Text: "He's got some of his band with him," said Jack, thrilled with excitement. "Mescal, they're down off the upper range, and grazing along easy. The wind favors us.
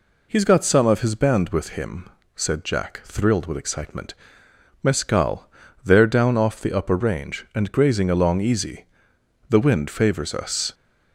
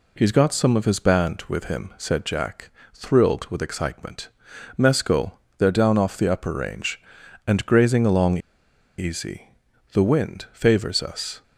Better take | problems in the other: first | pauses between "along" and "easy"; noticeable; at 8.3 s; 0.59 s long

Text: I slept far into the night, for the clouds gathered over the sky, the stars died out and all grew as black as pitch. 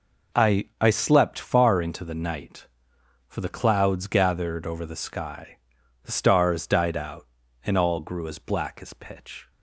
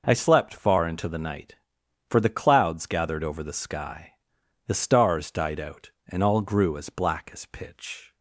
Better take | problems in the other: second | says "I" twice; at 0.8 s

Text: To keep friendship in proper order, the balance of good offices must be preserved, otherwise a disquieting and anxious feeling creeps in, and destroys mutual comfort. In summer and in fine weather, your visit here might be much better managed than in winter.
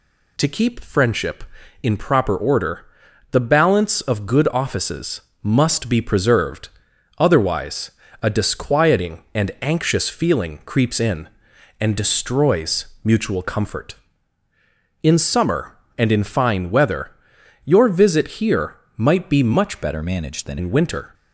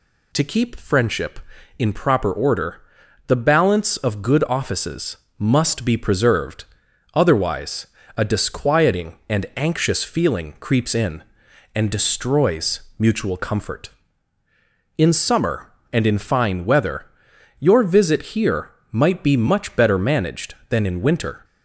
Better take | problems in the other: second | pauses between "offices" and "must"; slight; at 5.2 s; 0.20 s long; slight in the second // pauses between "otherwise" and "a"; slight; at 7.9 s; 0.30 s long; slight in the second // pauses between "destroys" and "mutual"; slight; at 12.8 s; 0.18 s long; slight in the second // pauses between "here" and "might"; slight; at 18.7 s; 0.20 s long; slight in the second // changes voice from "better" to "than"; from 19.8 to 20.5 s; 0.7 s long

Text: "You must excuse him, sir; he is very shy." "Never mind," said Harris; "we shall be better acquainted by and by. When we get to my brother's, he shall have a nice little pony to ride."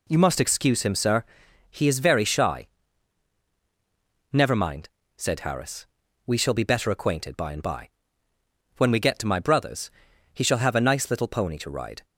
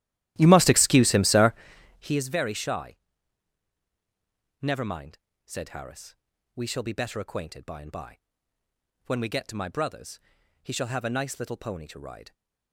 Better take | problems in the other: first | starts louder than the rest; strong; until 2.3 s; 14 dB

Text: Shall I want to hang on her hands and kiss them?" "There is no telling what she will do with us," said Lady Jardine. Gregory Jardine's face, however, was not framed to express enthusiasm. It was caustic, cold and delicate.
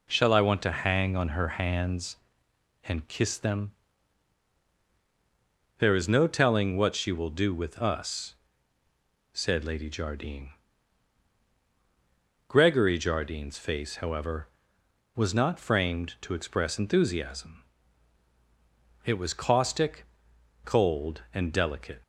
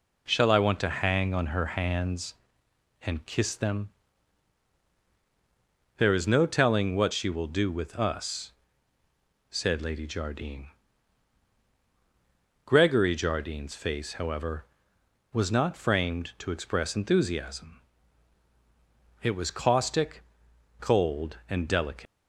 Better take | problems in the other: first | leaves "delicate" unfinished; at 22.0 s; 120 ms

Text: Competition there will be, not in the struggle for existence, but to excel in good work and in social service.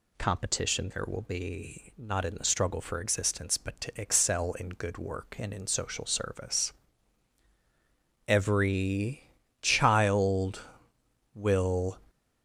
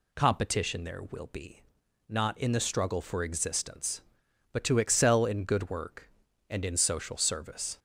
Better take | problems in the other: second | goes on to say "Every child will"; strong; from 8.2 s on; 3.7 s long

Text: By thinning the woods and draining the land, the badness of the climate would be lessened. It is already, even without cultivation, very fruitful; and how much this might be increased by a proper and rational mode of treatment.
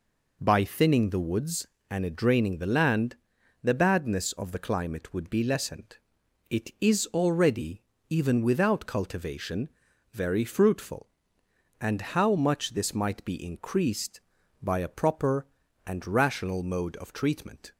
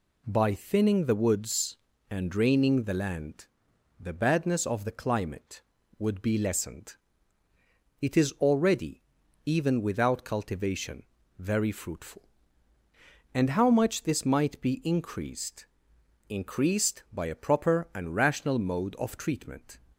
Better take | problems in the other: first | says "increased" twice; at 16.2 s

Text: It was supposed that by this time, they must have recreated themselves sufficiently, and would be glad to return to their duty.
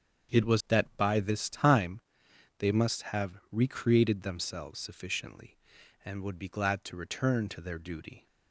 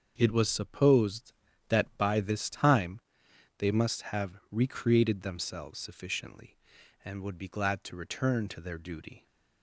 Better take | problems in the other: second | starts louder than the rest; strong; until 1.4 s; 7.5 dB; also in the second // skips "supposed"; at 0.6 s

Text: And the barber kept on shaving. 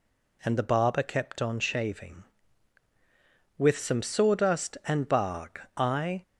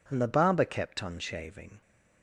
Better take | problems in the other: second | goes on to say "With some sawdust and bark I"; strong; from 3.5 s on; 2.6 s long

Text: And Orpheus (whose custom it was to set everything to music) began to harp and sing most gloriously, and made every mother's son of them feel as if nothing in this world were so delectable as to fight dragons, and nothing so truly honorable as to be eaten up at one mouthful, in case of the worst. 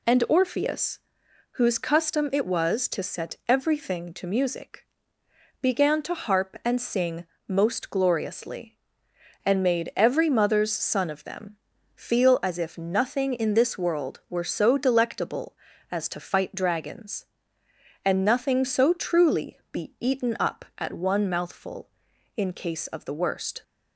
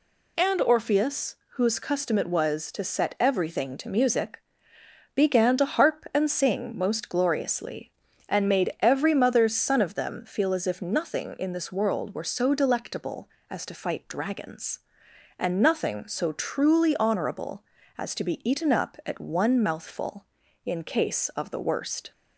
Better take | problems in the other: second | pauses between "sing" and "most"; slight; at 7.2 s; 0.22 s long // pauses between "them" and "feel"; at 11.5 s; 0.38 s long // skips "honorable as to"; at 19.6 s

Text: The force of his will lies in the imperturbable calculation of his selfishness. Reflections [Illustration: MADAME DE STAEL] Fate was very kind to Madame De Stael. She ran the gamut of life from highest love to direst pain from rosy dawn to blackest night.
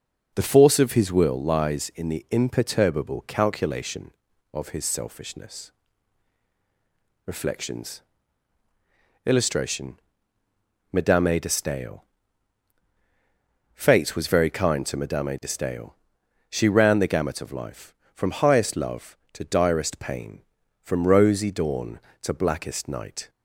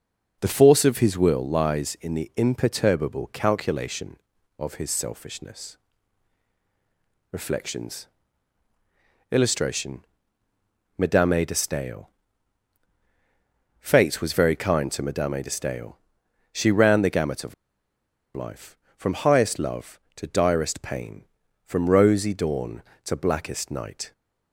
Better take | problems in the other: first | pauses between "Reflections" and "Illustration"; strong; at 8.0 s; 1.2 s long; strong in the first // pauses between "STAEL" and "Fate"; strong; at 12.0 s; 1.7 s long; strong in the first // pauses between "of" and "life"; noticeable; at 17.5 s; 0.81 s long

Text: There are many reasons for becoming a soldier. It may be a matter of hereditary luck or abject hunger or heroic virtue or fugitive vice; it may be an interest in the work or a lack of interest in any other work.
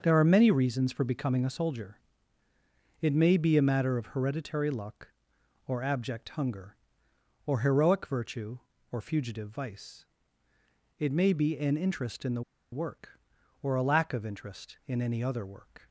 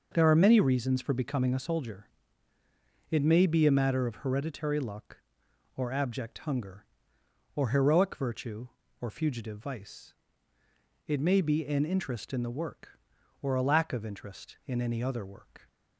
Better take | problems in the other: second | starts louder than the rest; until 1.0 s; 6 dB // pauses between "the" and "work"; slight; at 12.4 s; 0.31 s long

